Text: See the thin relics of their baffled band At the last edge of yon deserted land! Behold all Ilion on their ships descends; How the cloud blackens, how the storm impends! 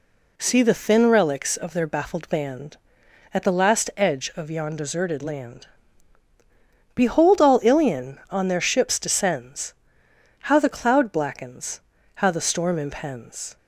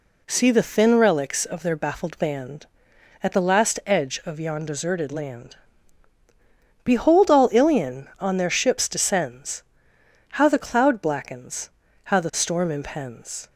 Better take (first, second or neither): neither